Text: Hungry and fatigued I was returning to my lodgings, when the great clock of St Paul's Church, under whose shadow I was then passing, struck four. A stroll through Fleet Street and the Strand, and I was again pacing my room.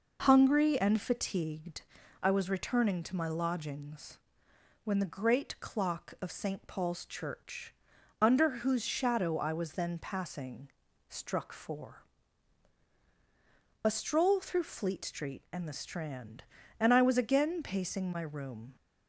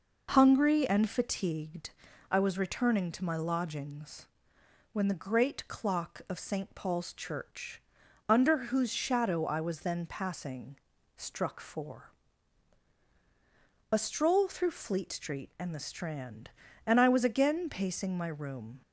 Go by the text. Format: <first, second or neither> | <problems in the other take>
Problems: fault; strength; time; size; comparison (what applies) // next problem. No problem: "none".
neither | pauses between "fatigued" and "I"; the same in both